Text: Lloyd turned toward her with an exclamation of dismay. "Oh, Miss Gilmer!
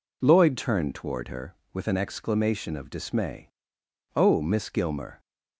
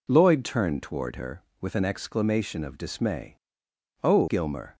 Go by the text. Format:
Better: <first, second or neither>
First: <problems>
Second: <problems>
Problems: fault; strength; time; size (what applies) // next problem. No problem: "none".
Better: first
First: none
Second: skips "Miss"; at 4.2 s